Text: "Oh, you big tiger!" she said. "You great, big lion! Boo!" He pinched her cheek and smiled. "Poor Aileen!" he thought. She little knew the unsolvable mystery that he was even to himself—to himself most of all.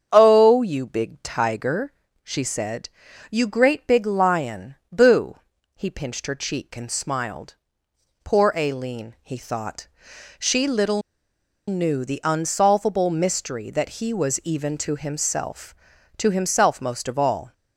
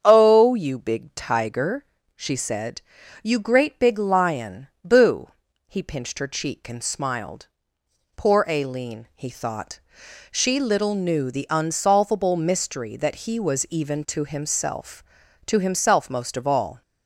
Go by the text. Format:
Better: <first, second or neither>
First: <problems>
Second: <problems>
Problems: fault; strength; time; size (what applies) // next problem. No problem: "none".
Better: second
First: starts louder than the rest; strong; until 1.1 s; 7.5 dB // pauses between "little" and "knew"; noticeable; at 11.0 s; 0.67 s long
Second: starts louder than the rest; strong; until 1.0 s; 7.5 dB